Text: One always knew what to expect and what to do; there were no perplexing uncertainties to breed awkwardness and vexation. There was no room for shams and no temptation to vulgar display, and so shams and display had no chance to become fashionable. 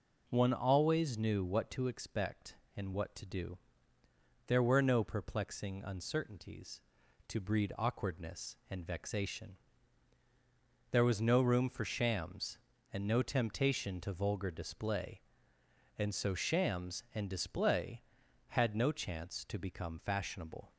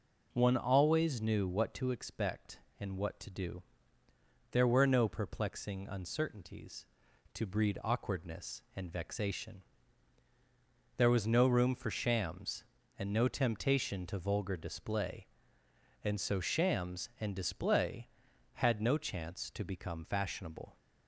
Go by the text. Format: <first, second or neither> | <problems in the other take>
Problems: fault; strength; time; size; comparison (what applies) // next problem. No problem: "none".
neither | none